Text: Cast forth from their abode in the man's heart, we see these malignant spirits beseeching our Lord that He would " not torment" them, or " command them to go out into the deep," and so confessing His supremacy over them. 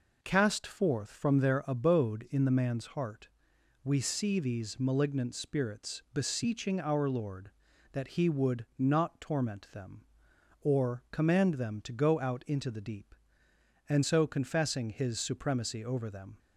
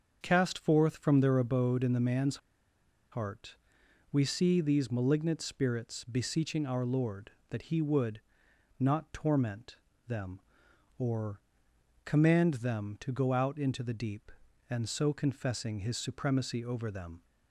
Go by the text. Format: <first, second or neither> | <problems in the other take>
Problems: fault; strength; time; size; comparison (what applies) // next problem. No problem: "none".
first | starts louder than the rest; until 1.2 s; 7 dB // pauses between "man's" and "heart"; noticeable; at 2.3 s; 0.73 s long // pauses between "torment" and "them"; slight; at 9.7 s; 0.28 s long